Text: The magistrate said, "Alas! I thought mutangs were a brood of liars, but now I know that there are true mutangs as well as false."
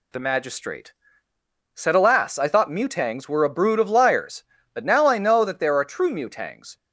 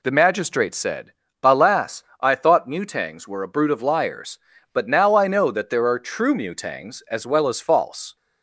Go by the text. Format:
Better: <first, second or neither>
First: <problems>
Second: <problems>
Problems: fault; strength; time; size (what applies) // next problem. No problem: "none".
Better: second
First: pauses between "magistrate" and "said"; noticeable; at 0.9 s; 0.80 s long // stops before "as well as false"; at 6.7 s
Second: none